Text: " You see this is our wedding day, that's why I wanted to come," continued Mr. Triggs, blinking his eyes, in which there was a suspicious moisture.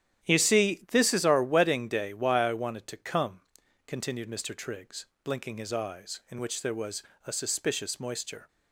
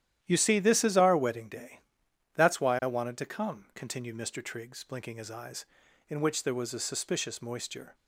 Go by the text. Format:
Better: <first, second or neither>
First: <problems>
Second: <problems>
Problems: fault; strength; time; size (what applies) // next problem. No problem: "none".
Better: second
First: starts louder than the rest; strong; until 1.3 s; 11 dB // skips "that's"; at 2.1 s // pauses between "was" and "a"; slight; at 7.0 s; 0.24 s long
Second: starts louder than the rest; strong; until 1.2 s; 11.5 dB